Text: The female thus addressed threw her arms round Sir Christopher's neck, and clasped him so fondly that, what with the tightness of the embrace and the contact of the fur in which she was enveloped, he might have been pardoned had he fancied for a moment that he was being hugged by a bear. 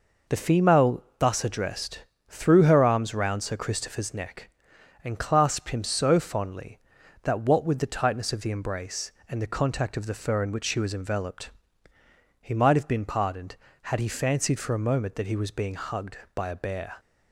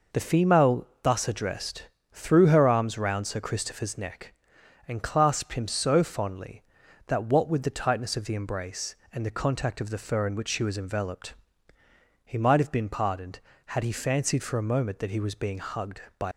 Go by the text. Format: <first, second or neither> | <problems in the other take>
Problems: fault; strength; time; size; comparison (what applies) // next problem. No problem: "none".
first | pauses between "female" and "thus"; slight; at 0.8 s; 0.16 s long; slight in the first // pauses between "addressed" and "threw"; slight; at 1.8 s; 0.24 s long; slight in the first // stops before "a bear"; at 16.3 s